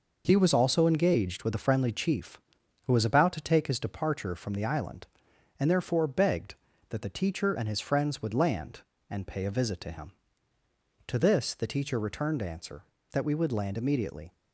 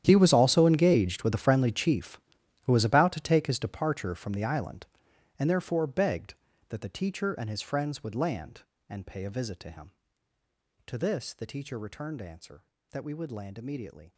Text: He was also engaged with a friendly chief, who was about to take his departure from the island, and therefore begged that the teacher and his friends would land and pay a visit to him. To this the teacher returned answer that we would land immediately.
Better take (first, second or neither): first